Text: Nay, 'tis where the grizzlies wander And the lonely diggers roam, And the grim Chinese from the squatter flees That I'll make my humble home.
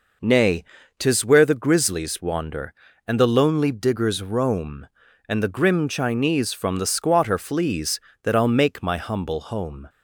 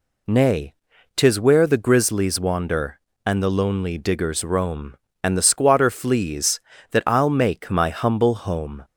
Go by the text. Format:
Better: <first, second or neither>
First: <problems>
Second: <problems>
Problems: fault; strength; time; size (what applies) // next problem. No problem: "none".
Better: first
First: none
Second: skips "grim Chinese from the"; at 5.4 s